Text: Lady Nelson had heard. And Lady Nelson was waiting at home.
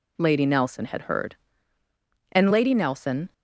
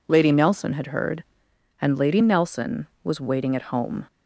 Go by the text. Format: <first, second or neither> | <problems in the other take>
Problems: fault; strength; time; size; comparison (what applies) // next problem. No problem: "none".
second | stops before "was waiting at home"; at 3.3 s